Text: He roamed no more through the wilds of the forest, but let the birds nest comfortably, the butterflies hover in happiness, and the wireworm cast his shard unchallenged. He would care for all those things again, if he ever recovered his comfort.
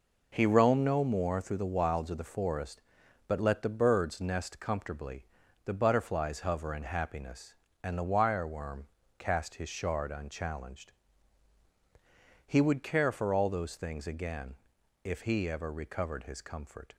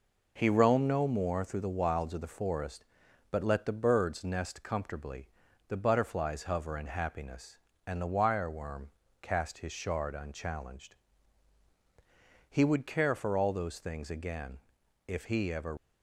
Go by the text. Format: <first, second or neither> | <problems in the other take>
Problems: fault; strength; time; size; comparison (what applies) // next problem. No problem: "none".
first | pauses between "wireworm" and "cast"; slight; at 8.8 s; 0.34 s long; slight in the first // stops before "recovered his comfort"; at 15.7 s